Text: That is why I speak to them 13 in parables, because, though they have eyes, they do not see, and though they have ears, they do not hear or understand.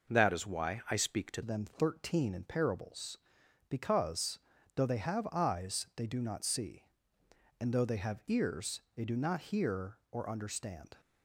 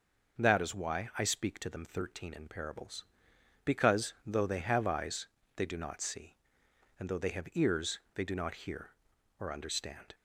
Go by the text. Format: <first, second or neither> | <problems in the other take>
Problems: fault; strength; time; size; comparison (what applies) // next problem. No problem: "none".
second | changes voice at "them"; from 1.4 s on; 9.5 s long